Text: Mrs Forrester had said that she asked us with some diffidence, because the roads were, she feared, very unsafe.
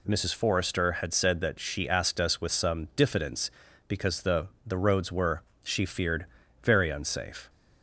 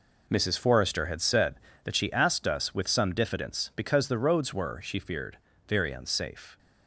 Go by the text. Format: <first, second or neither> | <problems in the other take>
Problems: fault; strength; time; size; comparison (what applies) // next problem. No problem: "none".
second | says "the" twice; at 4.6 s